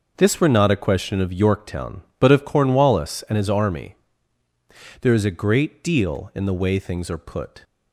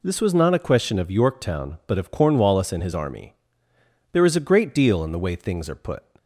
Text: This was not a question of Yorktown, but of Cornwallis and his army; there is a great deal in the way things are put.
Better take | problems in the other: second | says "were" for "was"; at 0.3 s

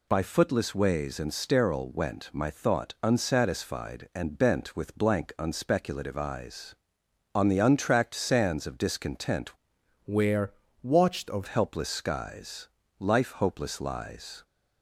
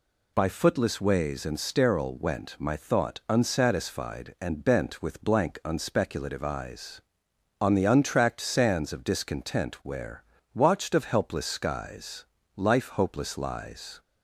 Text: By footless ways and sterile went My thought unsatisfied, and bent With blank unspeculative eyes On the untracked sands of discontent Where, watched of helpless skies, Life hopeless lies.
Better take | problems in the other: second | changes voice from "Where" to "of"; from 10.0 to 11.4 s; 1.4 s long

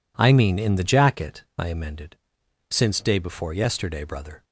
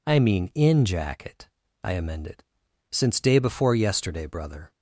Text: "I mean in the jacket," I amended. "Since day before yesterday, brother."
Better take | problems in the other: first | skips "the"; at 0.8 s

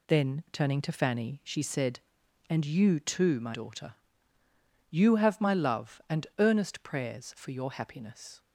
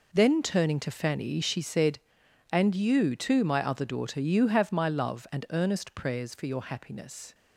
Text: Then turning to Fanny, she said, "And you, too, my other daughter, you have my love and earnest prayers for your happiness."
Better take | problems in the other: second | skips "other"; at 3.5 s

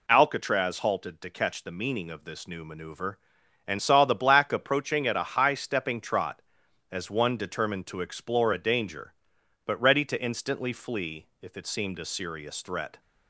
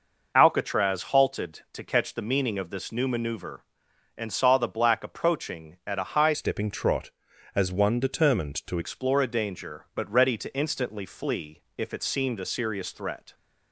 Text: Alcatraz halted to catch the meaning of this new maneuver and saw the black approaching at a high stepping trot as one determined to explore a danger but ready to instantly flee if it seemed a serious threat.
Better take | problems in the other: first | changes voice from "stepping" to "to"; from 6.3 to 8.7 s; 2.4 s long // pauses between "flee" and "if"; slight; at 11.6 s; 0.16 s long; slight in the first

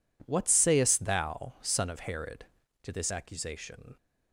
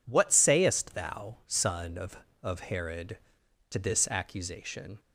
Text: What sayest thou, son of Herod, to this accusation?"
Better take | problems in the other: first | says "of" twice; at 2.3 s

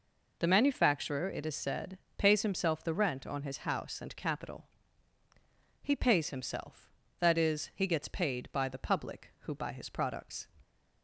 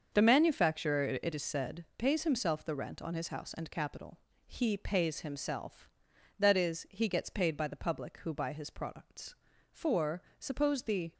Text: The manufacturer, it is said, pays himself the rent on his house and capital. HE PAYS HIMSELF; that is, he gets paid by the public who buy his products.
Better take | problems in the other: first | starts louder than the rest; until 1.1 s; 6.5 dB // goes on to say "For suppose the"; from 9.7 s on; 1.4 s long

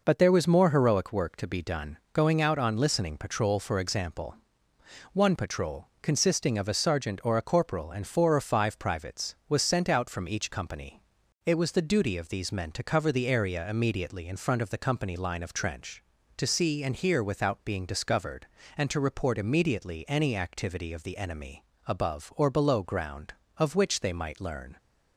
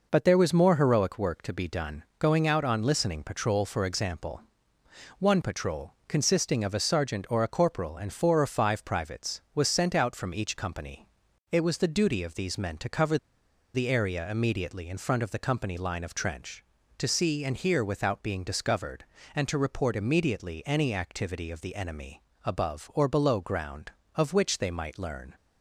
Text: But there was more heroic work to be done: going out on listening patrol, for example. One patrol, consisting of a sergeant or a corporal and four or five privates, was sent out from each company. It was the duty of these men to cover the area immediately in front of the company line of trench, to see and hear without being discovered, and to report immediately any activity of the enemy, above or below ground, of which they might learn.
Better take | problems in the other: first | pauses between "cover" and "the"; noticeable; at 13.1 s; 0.58 s long

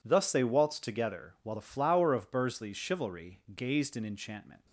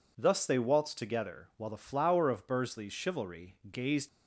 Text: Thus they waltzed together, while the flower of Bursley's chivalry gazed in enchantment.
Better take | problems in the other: first | stops before "in enchantment"; at 4.0 s

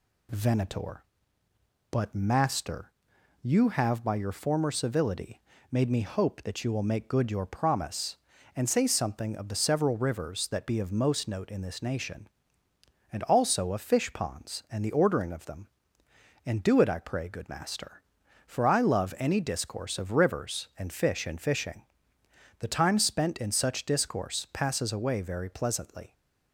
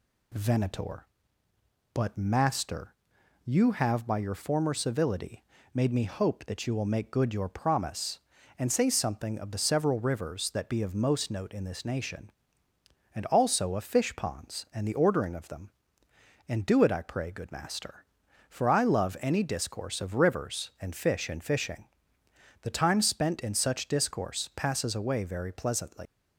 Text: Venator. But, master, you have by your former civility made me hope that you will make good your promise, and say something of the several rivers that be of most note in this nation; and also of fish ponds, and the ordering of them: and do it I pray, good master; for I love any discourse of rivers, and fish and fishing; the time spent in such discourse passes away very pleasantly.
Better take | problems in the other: first | pauses between "civility" and "made"; slight; at 5.4 s; 0.32 s long; slight in the first // leaves "pleasantly" unfinished; at 26.0 s; 115 ms

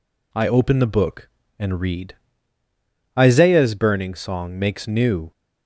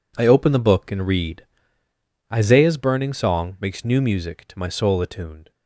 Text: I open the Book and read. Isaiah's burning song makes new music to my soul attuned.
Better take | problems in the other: second | stops before "music to my soul attuned"; at 5.3 s

